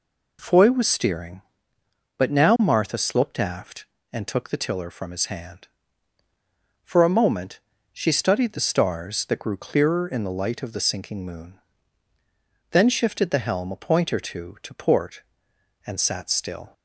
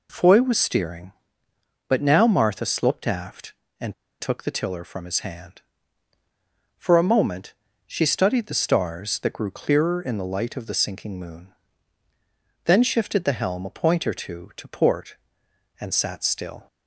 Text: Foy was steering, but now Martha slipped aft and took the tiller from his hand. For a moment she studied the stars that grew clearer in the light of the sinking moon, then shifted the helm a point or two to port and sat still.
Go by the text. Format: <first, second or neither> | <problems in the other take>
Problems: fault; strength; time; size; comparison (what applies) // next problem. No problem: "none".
first | pauses between "and" and "took"; slight; at 3.9 s; 0.26 s long // pauses between "moment" and "she"; slight; at 7.5 s; 0.32 s long; slight in the first